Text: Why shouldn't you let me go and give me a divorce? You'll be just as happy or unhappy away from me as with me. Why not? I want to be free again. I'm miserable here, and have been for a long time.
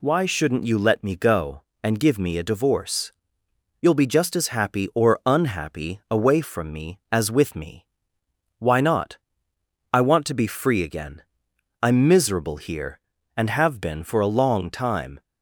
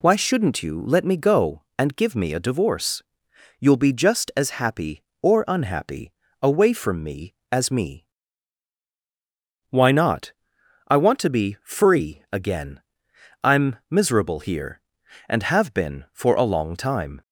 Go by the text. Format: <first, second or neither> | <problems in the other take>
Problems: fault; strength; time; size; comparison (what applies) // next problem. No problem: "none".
first | pauses between "unhappy" and "away"; slight; at 6.1 s; 0.30 s long // skips "with"; at 7.6 s